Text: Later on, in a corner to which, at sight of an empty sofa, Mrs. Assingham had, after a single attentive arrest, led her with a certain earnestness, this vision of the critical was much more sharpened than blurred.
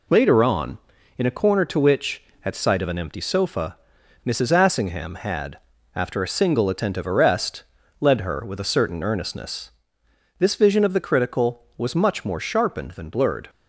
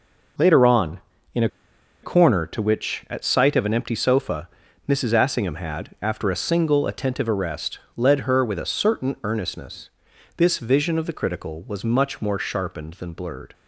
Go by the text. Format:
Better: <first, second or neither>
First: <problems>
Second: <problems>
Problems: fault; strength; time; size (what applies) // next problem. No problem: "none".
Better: first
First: none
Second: pauses between "a" and "corner"; noticeable; at 1.4 s; 0.54 s long